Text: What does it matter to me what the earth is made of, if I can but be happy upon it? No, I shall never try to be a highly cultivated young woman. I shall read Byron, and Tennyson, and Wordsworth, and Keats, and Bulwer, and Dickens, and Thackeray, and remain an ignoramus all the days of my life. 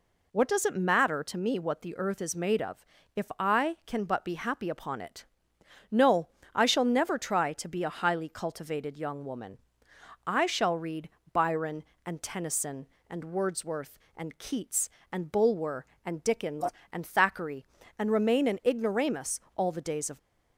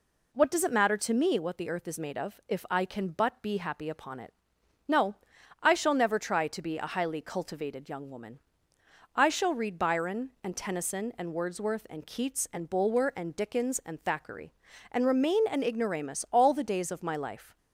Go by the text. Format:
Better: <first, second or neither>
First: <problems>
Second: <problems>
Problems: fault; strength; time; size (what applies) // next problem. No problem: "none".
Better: second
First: pauses between "read" and "Byron"; slight; at 11.0 s; 0.22 s long // pauses between "ignoramus" and "all"; slight; at 19.3 s; 0.16 s long // stops before "my life"; at 20.1 s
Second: none